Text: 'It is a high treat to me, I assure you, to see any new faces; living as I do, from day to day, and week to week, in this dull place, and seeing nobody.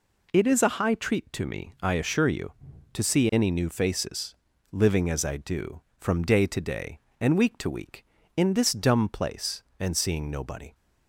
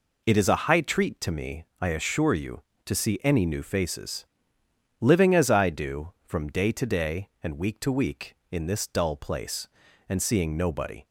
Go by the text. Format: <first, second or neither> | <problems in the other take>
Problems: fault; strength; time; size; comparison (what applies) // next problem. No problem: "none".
second | says "dumb" for "dull"; at 8.7 s